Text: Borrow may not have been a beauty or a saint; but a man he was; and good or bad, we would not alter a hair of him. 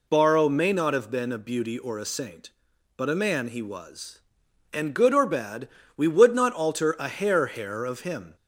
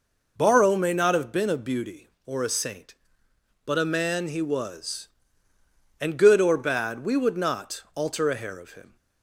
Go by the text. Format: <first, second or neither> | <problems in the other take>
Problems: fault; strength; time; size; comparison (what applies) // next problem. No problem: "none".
second | says "hair" twice; at 7.4 s